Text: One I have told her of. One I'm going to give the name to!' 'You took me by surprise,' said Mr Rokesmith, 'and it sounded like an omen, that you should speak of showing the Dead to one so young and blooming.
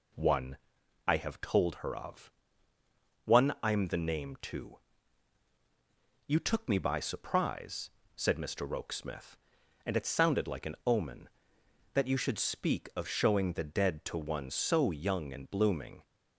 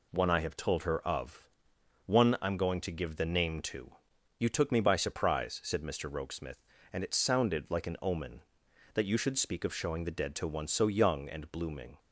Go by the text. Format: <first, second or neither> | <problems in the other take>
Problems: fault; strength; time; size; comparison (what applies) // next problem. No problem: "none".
second | pauses between "One" and "I"; noticeable; at 0.5 s; 0.50 s long // skips "going to give"; at 3.8 s